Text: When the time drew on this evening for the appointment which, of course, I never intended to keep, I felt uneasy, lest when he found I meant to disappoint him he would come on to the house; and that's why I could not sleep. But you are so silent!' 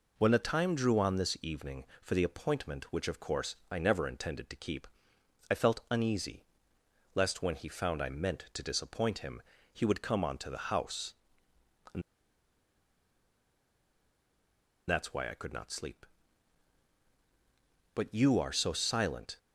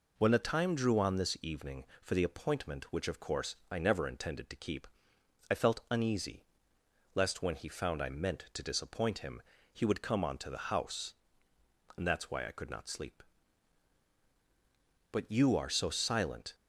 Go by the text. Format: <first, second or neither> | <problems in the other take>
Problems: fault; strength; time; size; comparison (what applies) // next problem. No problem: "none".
second | pauses between "him" and "he"; slight; at 9.4 s; 0.32 s long; slight in the second // pauses between "and" and "that's"; strong; at 12.0 s; 2.8 s long